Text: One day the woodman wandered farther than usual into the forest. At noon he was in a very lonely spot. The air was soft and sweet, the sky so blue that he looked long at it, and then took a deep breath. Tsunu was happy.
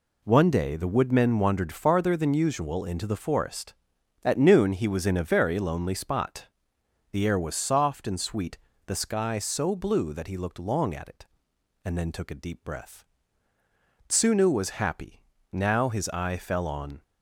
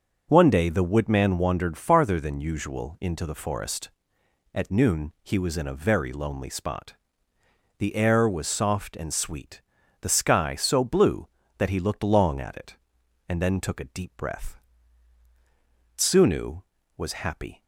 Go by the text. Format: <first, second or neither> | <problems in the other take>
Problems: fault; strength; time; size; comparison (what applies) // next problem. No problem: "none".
second | goes on to say "Now his eye fell on"; from 15.5 s on; 1.5 s long